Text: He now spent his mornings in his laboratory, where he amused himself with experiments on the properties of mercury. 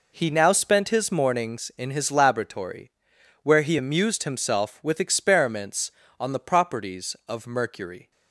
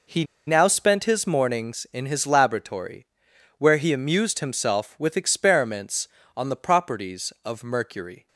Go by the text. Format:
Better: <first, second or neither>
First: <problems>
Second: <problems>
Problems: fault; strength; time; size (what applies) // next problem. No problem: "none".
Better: first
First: none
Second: pauses between "He" and "now"; slight; at 0.2 s; 0.22 s long